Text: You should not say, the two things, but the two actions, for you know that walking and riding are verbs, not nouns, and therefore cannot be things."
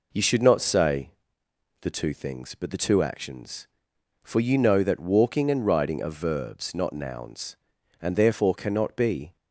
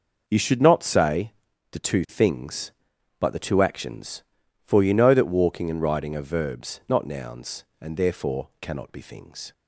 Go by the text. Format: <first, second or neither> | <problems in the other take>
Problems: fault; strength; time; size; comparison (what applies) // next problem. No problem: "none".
second | stops before "things"; at 9.3 s